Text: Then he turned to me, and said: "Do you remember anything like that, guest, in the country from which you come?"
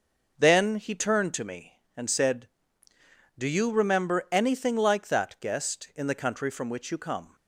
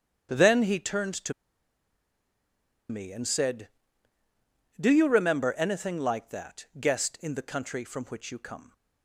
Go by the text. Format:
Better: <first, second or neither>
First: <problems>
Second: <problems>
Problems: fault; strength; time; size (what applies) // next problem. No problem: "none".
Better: first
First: starts louder than the rest; noticeable; until 1.4 s; 6 dB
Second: starts louder than the rest; strong; until 1.3 s; 8 dB // pauses between "to" and "me"; strong; at 1.3 s; 1.5 s long